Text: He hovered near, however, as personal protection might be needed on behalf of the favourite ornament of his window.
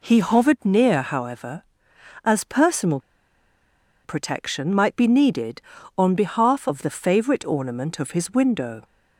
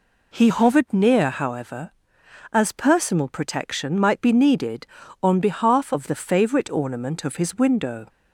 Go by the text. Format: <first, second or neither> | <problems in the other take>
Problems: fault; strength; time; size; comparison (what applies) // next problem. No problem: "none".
second | pauses between "personal" and "protection"; at 2.9 s; 1.0 s long